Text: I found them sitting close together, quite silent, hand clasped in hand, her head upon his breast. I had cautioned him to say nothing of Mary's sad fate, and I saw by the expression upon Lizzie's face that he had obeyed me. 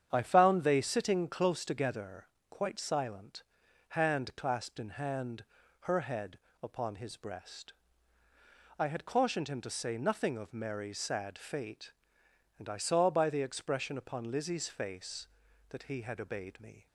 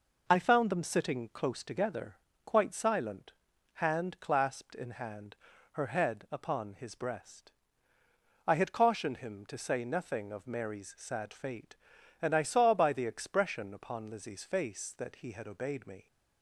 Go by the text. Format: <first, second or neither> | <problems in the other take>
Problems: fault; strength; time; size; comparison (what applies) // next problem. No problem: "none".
second | starts louder than the rest; strong; until 1.1 s; 8.5 dB // says "they" for "them"; at 0.6 s // pauses between "head" and "upon"; slight; at 6.3 s; 0.26 s long